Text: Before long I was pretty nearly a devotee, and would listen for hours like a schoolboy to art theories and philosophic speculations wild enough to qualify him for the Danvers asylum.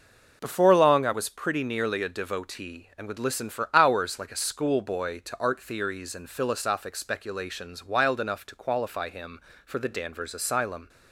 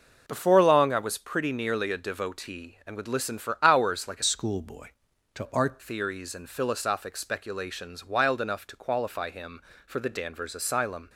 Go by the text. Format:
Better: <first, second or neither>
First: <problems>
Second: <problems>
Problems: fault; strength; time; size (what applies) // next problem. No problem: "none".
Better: first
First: none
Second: changes voice from "schoolboy" to "art"; from 4.2 to 5.8 s; 1.6 s long